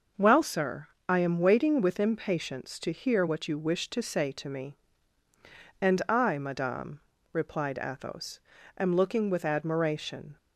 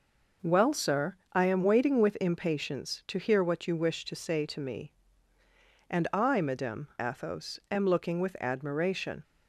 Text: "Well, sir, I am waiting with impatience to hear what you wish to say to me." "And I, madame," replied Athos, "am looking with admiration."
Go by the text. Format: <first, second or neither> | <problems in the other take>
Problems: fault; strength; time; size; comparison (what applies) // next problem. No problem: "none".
first | skips "replied"; at 6.9 s